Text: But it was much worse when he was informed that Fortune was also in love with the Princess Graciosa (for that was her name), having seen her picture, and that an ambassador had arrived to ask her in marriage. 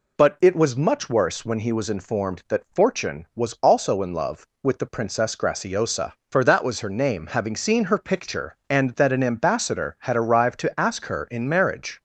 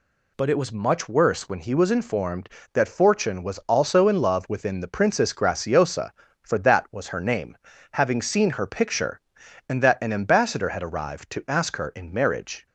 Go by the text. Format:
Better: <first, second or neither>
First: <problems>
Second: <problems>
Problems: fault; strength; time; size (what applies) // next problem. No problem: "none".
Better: first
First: none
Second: says "within" for "with"; at 4.4 s